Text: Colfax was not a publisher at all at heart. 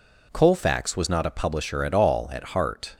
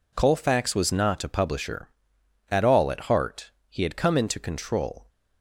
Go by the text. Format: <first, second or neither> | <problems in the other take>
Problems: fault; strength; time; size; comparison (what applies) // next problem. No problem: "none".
first | goes on to say "He had come into control"; from 3.6 s on; 1.4 s long